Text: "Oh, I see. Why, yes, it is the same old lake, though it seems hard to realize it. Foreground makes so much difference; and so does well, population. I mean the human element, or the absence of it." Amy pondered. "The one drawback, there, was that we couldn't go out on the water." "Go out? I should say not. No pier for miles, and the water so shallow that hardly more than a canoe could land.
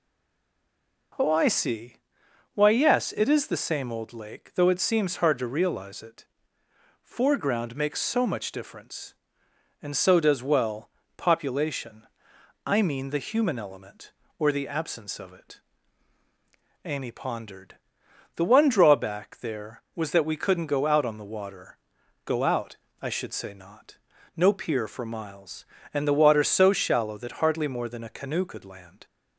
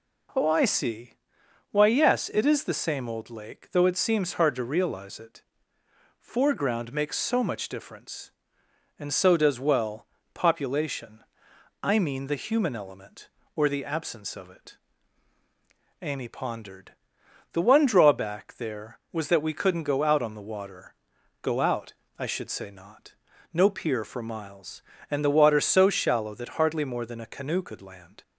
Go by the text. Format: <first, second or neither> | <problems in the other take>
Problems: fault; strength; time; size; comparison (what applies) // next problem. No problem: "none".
second | stays silent before the first word; until 1.1 s; 1.1 s long